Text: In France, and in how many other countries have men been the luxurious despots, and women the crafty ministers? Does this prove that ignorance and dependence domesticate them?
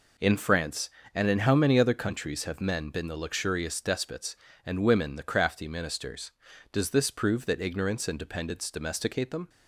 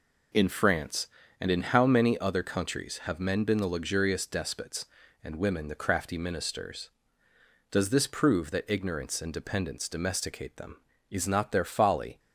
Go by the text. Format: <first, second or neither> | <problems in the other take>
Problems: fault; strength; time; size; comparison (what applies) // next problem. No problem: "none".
first | goes on to say "Is not their folly"; noticeable; from 11.0 s on; 1.1 s long